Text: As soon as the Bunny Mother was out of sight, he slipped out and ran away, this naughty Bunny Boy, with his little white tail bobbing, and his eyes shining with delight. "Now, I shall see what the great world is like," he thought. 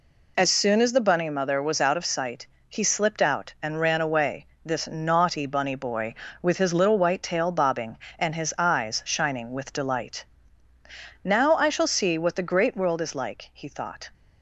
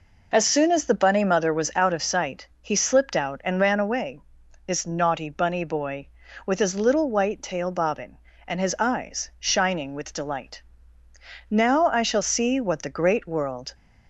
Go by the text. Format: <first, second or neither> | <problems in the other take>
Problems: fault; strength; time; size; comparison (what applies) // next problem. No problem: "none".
first | stops before "is like he thought"; at 13.7 s